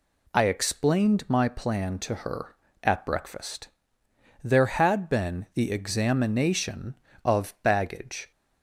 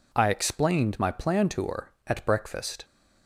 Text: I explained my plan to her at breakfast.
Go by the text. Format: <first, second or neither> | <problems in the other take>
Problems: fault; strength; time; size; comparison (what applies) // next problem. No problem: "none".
second | goes on to say "There had been the examination of baggage"; strong; from 4.4 s on; 3.8 s long